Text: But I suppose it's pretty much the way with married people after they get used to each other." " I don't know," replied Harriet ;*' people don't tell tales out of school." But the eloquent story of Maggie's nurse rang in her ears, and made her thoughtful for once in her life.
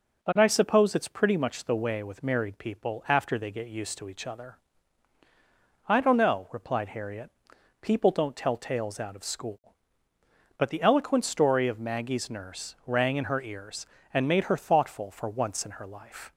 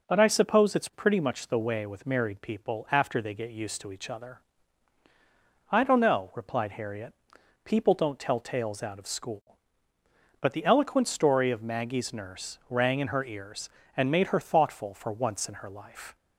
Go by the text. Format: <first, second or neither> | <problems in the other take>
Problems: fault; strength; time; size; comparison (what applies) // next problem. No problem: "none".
neither | starts louder than the rest; the same in both